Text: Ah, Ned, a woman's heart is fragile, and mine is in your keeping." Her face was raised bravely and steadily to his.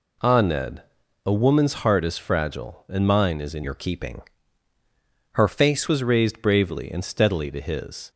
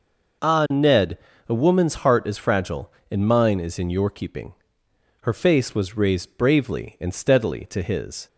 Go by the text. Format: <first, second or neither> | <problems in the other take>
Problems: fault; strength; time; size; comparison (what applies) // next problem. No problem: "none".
second | changes voice from "your" to "face"; from 3.6 to 5.8 s; 2.2 s long